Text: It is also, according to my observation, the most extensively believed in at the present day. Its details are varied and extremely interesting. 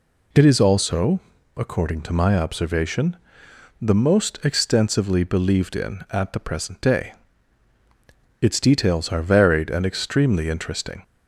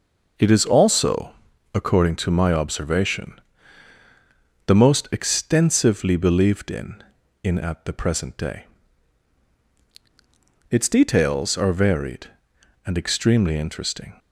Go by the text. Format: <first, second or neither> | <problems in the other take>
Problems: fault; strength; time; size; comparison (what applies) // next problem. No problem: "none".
first | says "in" twice; at 7.4 s